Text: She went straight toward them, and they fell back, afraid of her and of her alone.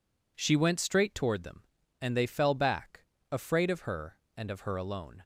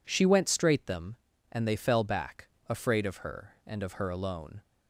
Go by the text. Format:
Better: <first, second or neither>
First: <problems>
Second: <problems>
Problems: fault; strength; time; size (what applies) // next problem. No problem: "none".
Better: first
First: none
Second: skips "toward"; at 0.8 s